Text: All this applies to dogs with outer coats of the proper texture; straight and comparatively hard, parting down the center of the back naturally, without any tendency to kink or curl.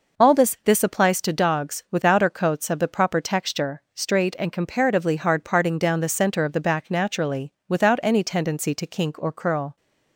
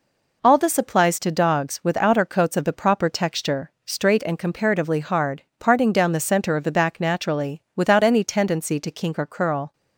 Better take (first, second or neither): second